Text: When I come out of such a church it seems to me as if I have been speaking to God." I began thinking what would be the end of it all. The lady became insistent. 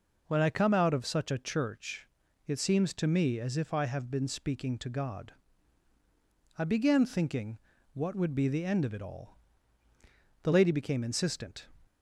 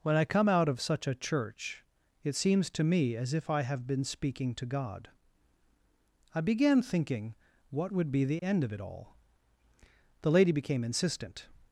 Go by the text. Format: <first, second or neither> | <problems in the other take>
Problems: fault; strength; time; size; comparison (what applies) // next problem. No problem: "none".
neither | pauses between "church" and "it"; the same in both // pauses between "thinking" and "what"; slight; the same in both